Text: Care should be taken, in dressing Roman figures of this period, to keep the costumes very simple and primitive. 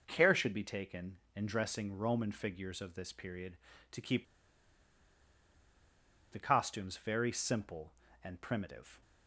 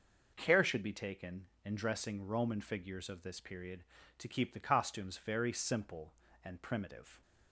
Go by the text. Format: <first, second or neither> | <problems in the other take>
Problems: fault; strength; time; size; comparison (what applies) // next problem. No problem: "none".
second | pauses between "keep" and "the"; strong; at 4.2 s; 2.0 s long